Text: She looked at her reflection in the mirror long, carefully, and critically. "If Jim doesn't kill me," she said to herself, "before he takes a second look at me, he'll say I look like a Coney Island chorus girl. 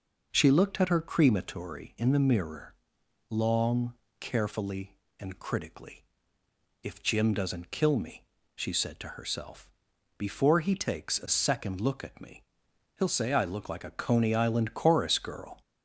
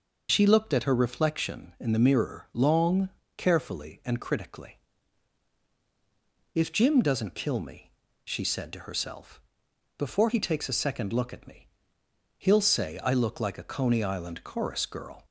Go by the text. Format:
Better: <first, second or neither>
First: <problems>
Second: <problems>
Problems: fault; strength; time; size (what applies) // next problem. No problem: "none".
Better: second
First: says "crematory" for "reflection"; at 1.0 s // pauses between "mirror" and "long"; noticeable; at 2.7 s; 0.58 s long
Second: none